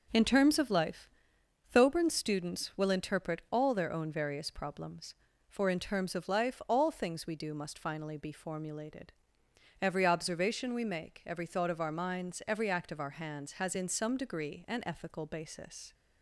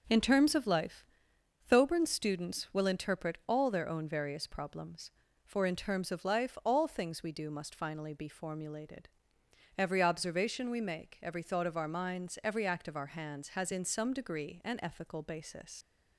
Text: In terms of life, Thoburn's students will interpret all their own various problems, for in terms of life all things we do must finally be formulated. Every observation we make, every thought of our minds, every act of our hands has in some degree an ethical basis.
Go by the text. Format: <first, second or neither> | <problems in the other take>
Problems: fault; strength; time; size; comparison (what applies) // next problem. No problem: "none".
first | leaves "basis" unfinished; at 15.8 s; 85 ms